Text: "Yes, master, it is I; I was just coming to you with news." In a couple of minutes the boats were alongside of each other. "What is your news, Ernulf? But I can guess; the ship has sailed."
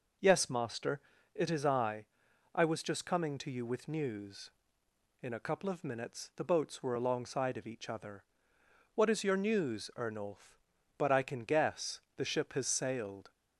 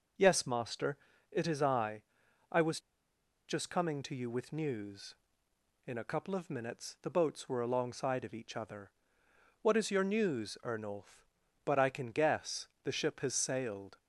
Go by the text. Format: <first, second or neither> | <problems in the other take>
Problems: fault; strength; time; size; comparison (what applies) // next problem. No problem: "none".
first | pauses between "was" and "just"; noticeable; at 2.7 s; 0.68 s long